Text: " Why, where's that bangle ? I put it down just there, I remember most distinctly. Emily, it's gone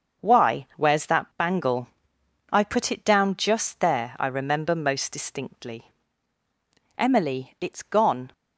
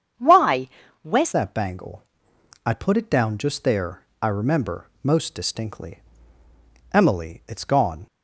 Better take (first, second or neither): first